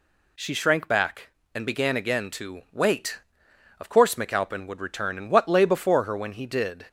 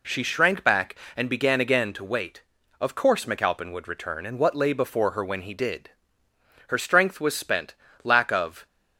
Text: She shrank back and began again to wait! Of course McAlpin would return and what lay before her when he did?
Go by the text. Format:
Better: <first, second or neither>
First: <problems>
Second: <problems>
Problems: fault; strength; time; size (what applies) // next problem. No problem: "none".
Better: first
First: none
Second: goes on to say "Her strength was spent lack of"; strong; from 6.6 s on; 1.9 s long